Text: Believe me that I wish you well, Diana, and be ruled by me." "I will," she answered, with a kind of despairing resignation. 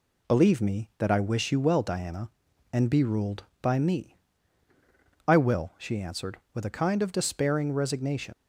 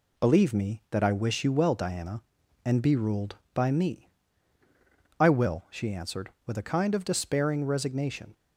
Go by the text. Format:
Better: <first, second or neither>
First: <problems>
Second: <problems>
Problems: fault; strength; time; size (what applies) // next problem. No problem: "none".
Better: second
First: leaves "resignation" unfinished; at 8.3 s; 70 ms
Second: none